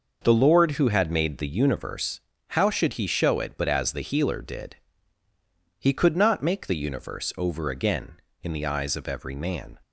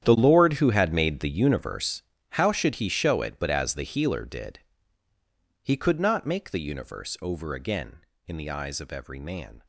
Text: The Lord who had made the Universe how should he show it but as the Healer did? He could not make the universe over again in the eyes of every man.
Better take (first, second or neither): first